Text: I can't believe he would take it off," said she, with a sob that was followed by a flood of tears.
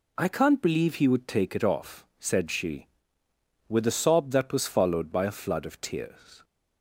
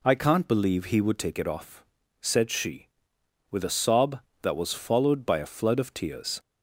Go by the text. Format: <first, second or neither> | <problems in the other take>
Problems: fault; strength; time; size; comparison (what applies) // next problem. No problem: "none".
neither | none